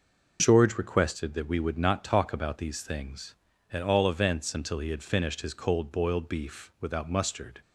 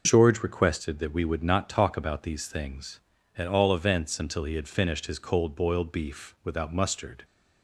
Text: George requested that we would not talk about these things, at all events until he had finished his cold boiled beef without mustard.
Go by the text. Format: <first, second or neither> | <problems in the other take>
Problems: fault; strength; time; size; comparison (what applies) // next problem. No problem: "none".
neither | none